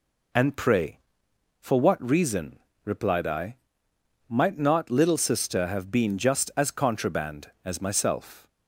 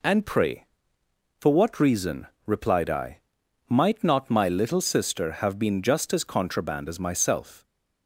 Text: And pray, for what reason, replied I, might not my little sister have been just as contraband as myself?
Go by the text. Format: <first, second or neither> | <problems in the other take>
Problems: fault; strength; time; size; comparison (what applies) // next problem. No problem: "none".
second | skips "my"; at 4.8 s